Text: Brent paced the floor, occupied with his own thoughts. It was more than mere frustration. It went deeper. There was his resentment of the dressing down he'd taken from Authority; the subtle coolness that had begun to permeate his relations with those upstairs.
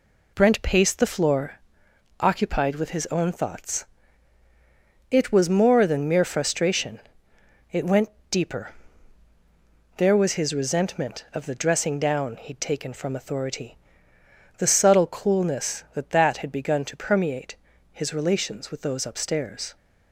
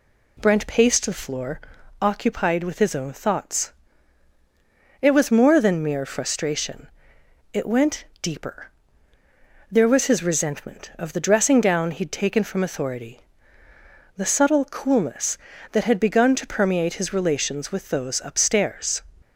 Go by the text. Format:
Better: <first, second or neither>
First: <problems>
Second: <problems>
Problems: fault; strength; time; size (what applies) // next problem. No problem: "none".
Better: second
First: pauses between "went" and "deeper"; slight; at 8.0 s; 0.22 s long // says "that" twice; at 16.0 s // pauses between "permeate" and "his"; slight; at 17.5 s; 0.36 s long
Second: pauses between "went" and "deeper"; slight; at 8.0 s; 0.18 s long